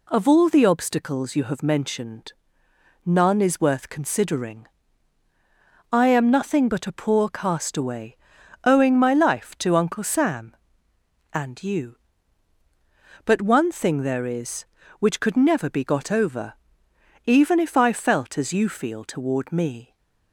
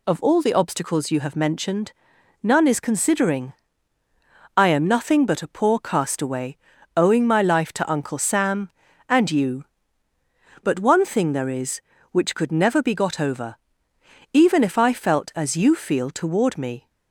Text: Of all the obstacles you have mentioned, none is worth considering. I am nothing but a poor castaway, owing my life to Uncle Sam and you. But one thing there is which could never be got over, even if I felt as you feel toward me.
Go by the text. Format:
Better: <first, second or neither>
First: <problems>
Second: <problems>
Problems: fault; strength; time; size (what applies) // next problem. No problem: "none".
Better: first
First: none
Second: skips "worth"; at 2.8 s